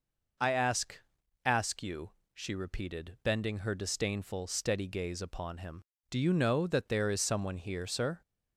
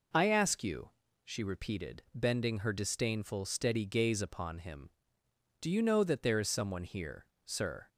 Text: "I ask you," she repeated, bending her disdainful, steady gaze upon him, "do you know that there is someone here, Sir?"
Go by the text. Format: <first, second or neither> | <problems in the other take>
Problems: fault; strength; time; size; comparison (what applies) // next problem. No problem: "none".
second | says "ask" twice; at 1.4 s